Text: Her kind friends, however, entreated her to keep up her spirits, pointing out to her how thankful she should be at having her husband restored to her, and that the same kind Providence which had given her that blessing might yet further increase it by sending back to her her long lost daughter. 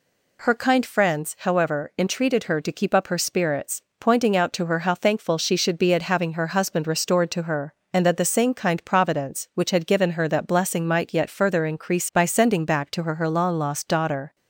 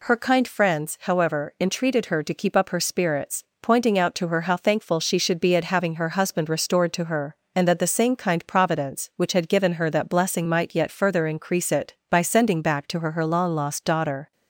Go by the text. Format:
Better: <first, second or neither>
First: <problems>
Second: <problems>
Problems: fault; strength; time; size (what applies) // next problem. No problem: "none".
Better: second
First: skips "it"; at 12.1 s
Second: none